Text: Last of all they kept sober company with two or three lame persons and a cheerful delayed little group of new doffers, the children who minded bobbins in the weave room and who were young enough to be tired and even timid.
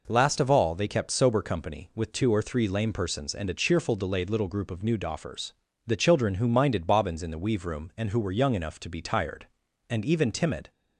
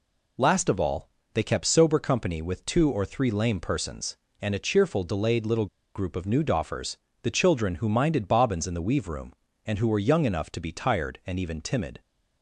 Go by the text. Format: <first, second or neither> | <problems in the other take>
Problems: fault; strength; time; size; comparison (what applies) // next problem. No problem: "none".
first | pauses between "all" and "they"; slight; at 1.0 s; 0.26 s long // pauses between "little" and "group"; slight; at 5.6 s; 0.29 s long